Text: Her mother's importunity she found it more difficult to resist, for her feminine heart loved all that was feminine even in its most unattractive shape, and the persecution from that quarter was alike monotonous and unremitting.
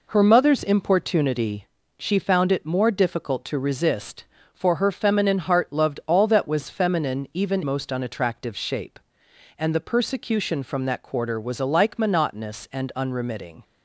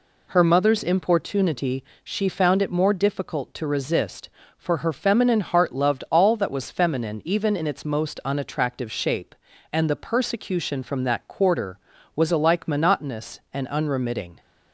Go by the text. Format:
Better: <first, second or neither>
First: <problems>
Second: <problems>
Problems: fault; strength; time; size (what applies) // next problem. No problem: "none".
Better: second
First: pauses between "importunity" and "she"; slight; at 1.6 s; 0.32 s long // skips "in its"; at 7.6 s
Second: pauses between "importunity" and "she"; slight; at 1.8 s; 0.20 s long